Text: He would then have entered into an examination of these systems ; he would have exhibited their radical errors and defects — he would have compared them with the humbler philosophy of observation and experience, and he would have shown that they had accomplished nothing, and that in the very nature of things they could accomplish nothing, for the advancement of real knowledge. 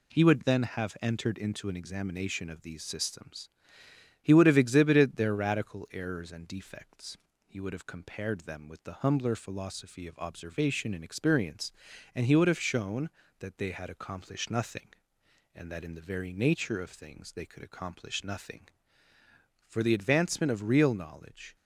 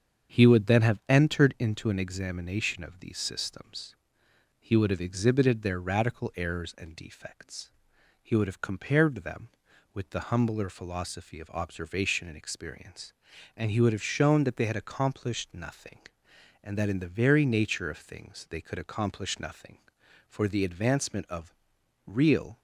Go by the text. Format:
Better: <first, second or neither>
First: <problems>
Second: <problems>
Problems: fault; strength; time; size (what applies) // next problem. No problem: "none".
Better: first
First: none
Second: starts louder than the rest; strong; until 1.4 s; 7 dB // pauses between "of" and "real"; noticeable; at 21.5 s; 0.50 s long // stops before "knowledge"; at 22.5 s